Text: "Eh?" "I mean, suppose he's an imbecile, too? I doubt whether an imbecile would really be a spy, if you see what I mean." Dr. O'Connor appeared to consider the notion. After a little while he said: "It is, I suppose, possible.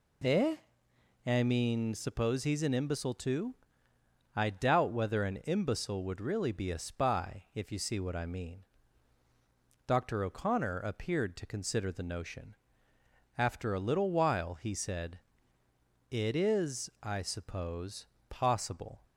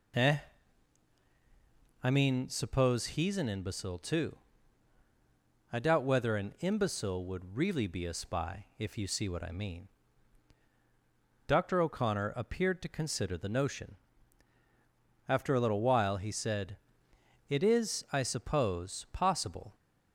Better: neither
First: none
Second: none

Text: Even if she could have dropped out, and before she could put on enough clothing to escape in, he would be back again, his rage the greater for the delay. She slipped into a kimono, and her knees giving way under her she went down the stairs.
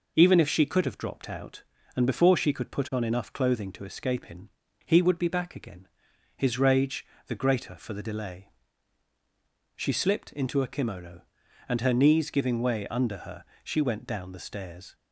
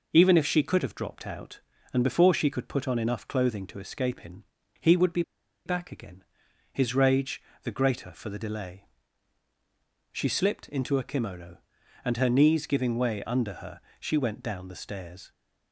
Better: first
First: pauses between "rage" and "the"; slight; at 7.0 s; 0.22 s long // pauses between "her" and "she"; slight; at 13.4 s; 0.18 s long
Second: pauses between "be" and "back"; at 5.2 s; 0.44 s long // pauses between "rage" and "the"; slight; at 7.4 s; 0.22 s long // pauses between "her" and "she"; slight; at 13.8 s; 0.18 s long

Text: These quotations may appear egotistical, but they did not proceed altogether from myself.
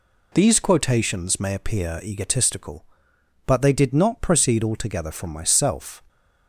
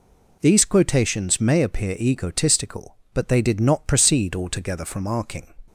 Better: first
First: none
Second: says "arcing" for "myself"; at 5.0 s

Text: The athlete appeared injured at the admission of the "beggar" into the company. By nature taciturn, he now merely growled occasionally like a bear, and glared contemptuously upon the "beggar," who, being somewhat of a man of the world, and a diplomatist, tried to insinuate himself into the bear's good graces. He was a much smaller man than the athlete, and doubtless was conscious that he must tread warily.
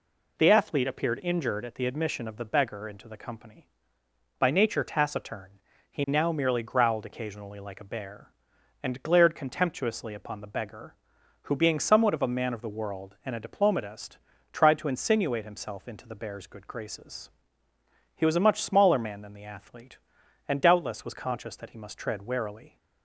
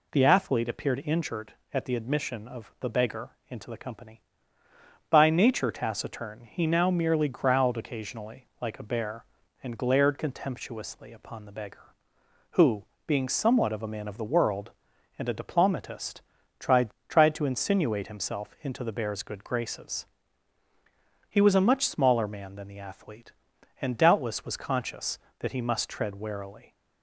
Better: first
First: none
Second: pauses between "beggar" and "into"; slight; at 3.2 s; 0.18 s long // says "tried" twice; at 17.1 s

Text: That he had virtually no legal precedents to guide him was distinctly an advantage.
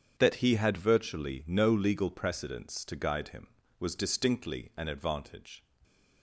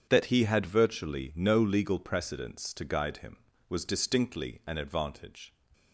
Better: neither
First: starts louder than the rest; strong; until 1.1 s; 8 dB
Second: starts louder than the rest; strong; until 1.1 s; 8 dB

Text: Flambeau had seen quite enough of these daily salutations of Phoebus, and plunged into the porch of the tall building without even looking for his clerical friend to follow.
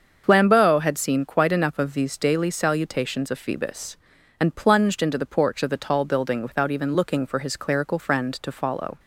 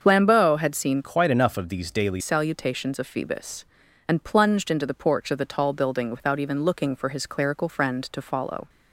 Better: first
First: starts louder than the rest; until 1.2 s; 6.5 dB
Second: starts louder than the rest; until 1.0 s; 6.5 dB // changes voice from "quite" to "daily"; from 1.0 to 2.2 s; 1.2 s long

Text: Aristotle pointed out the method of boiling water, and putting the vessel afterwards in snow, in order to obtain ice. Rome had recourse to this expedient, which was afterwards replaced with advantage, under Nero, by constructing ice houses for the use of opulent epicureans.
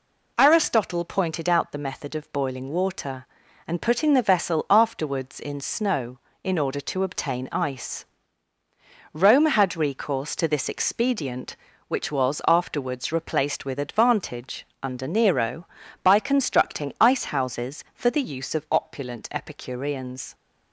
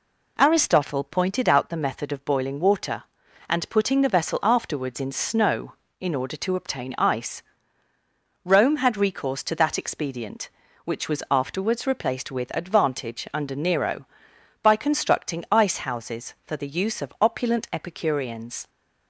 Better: first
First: none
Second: says "that" for "this"; at 9.5 s

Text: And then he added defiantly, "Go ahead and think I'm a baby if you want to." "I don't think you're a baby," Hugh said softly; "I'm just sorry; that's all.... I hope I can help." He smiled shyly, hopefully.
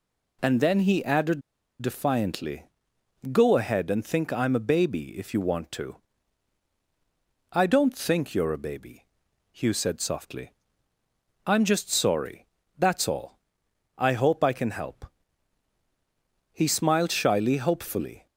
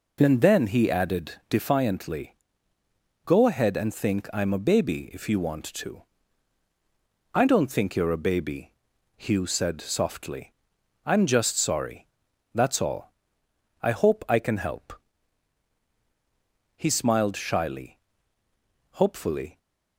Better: second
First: pauses between "added" and "defiantly"; at 1.4 s; 0.38 s long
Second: none

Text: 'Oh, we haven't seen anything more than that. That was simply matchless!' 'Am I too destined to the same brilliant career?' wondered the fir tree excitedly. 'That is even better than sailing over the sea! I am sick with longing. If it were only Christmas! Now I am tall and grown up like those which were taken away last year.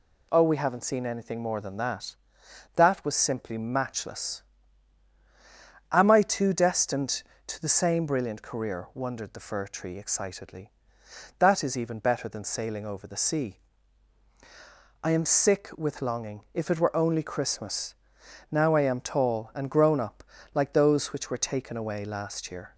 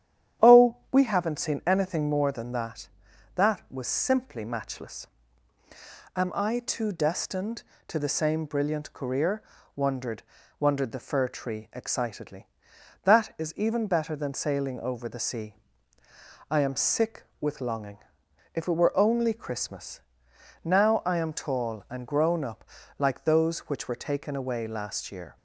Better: first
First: pauses between "up" and "like"; slight; at 20.2 s; 0.30 s long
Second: starts louder than the rest; strong; until 1.5 s; 10 dB // says "wondered" twice; at 10.5 s // pauses between "up" and "like"; slight; at 22.6 s; 0.32 s long

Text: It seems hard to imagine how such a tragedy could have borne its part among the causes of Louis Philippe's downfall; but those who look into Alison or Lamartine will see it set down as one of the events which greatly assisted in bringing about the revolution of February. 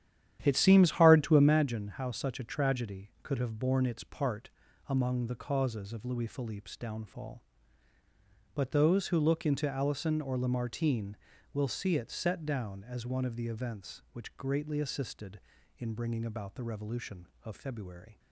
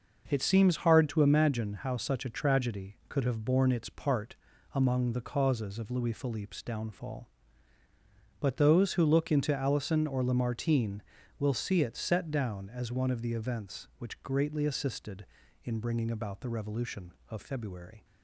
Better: second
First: starts louder than the rest; strong; until 1.7 s; 10.5 dB // pauses between "part" and "among"; at 4.4 s; 0.40 s long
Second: pauses between "part" and "among"; at 4.3 s; 0.40 s long

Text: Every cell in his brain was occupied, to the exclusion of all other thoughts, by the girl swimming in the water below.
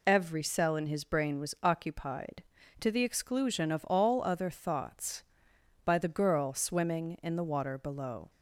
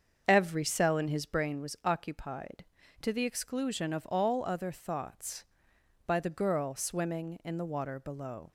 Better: first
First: none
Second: starts louder than the rest; until 1.5 s; 7 dB

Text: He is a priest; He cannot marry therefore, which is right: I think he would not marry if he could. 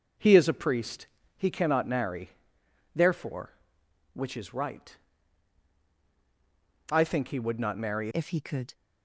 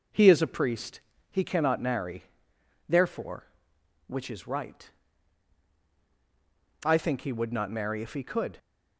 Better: second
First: pauses between "marry" and "therefore"; noticeable; at 2.3 s; 0.64 s long // changes voice at "if"; from 8.1 s on; 0.6 s long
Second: pauses between "marry" and "therefore"; noticeable; at 2.2 s; 0.64 s long

